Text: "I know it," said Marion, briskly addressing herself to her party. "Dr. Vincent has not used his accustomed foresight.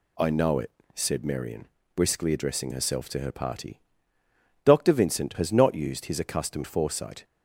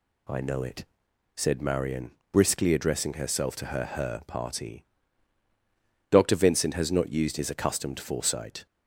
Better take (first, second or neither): first